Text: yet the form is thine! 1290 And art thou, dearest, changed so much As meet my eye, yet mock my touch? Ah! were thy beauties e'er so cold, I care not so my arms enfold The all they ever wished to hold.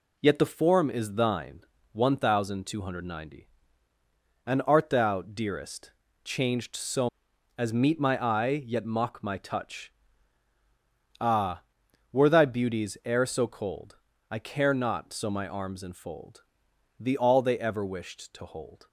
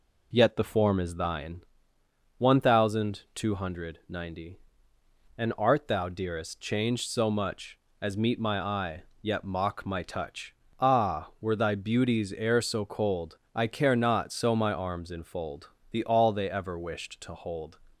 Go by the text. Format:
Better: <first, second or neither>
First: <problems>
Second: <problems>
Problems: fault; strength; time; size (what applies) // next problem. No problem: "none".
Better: second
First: skips "much"; at 7.3 s // pauses between "enfold" and "The"; noticeable; at 16.4 s; 0.56 s long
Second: pauses between "enfold" and "The"; slight; at 15.6 s; 0.24 s long